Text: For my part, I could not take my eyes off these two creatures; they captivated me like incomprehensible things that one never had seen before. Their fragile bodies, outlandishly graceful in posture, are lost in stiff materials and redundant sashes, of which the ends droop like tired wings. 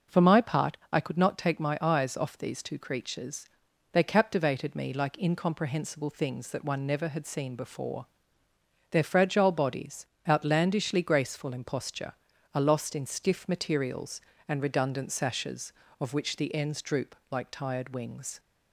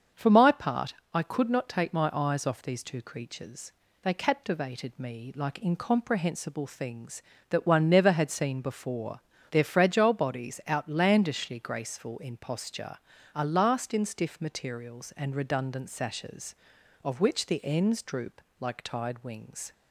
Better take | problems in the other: first | starts louder than the rest; until 1.3 s; 7 dB // says "last" for "lost"; at 13.4 s // pauses between "droop" and "like"; slight; at 18.4 s; 0.20 s long

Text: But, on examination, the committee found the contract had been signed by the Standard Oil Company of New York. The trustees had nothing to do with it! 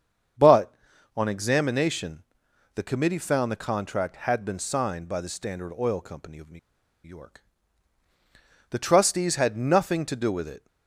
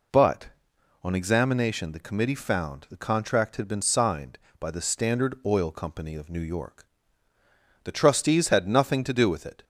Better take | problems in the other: second | starts louder than the rest; strong; until 1.8 s; 7.5 dB // pauses between "New" and "York"; at 6.5 s; 0.45 s long

